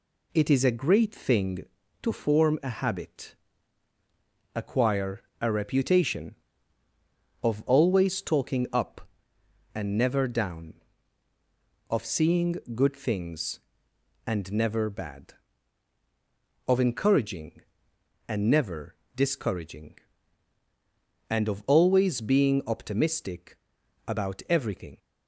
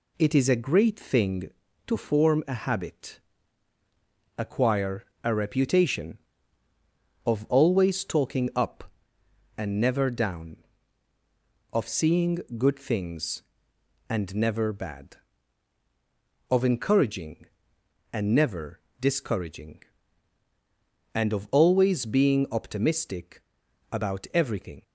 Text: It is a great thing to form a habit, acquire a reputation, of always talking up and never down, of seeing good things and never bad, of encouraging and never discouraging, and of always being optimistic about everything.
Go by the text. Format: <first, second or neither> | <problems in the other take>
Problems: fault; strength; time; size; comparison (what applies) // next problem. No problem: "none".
neither | pauses between "acquire" and "a"; slight; the same in both // pauses between "seeing" and "good"; slight; the same in both // pauses between "never" and "discouraging"; slight; the same in both // pauses between "optimistic" and "about"; noticeable; the same in both